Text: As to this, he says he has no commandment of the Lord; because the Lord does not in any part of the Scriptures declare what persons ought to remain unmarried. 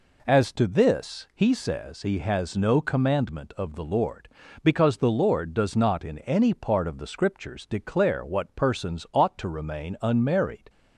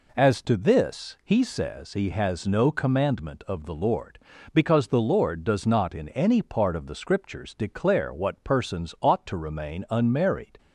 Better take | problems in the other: neither | none

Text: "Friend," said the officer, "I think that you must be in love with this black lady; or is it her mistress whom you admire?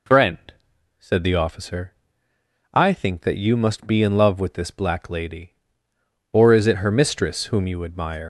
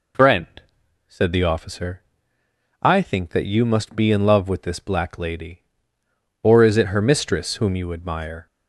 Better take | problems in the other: second | leaves "admire" unfinished; at 8.2 s; 90 ms

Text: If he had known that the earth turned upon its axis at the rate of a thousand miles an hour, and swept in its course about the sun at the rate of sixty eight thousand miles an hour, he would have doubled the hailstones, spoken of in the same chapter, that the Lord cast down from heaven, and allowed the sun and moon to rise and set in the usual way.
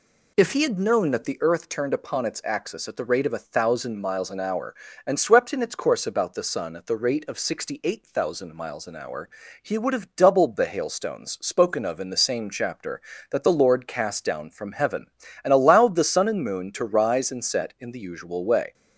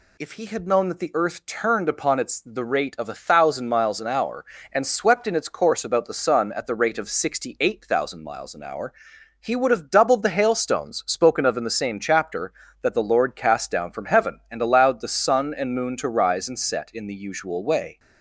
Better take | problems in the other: first | skips "axis at"; at 2.3 s

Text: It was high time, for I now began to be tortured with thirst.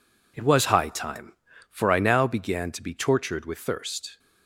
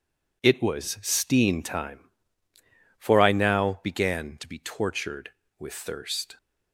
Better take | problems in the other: first | says "steen" for "high"; at 1.0 s

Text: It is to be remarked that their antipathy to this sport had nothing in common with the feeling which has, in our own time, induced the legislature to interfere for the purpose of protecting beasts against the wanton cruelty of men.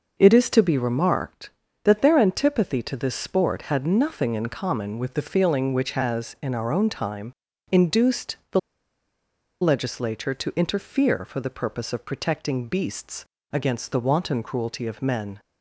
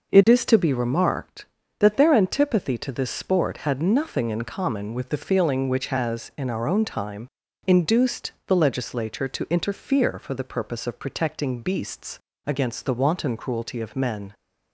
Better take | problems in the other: second | pauses between "the" and "legislature"; at 8.5 s; 1.0 s long // pauses between "beasts" and "against"; slight; at 13.2 s; 0.26 s long; slight in the second

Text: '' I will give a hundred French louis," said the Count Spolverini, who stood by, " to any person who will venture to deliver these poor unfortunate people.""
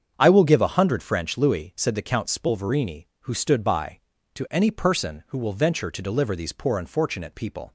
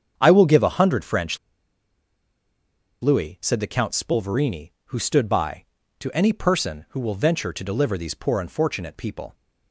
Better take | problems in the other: first | starts louder than the rest; strong; until 1.1 s; 7.5 dB; strong in the first // pauses between "French" and "louis"; strong; at 1.3 s; 1.6 s long

